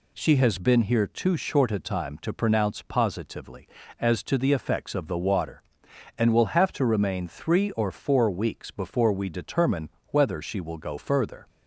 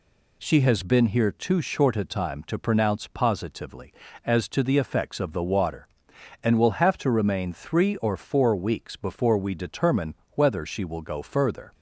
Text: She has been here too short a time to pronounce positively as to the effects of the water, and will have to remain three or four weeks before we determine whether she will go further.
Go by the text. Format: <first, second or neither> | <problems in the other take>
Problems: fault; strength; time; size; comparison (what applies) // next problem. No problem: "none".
neither | pauses between "determine" and "whether"; slight; the same in both